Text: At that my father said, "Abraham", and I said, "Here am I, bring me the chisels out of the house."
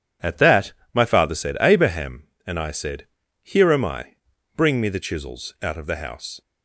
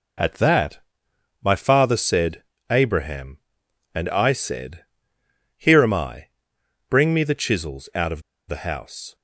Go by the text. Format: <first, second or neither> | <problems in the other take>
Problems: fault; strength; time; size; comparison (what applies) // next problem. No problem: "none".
first | pauses between "that" and "my"; noticeable; at 0.7 s; 0.64 s long; slight in the first // pauses between "of" and "the"; slight; at 8.2 s; 0.27 s long